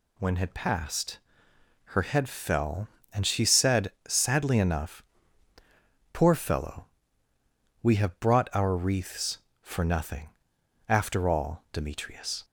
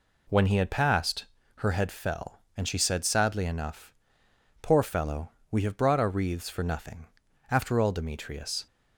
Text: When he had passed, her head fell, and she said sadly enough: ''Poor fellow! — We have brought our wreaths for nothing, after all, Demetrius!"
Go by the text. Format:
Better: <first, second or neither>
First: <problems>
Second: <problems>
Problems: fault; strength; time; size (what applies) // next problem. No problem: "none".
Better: second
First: skips "he"; at 0.3 s // pauses between "said" and "sadly"; slight; at 3.9 s; 0.16 s long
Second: none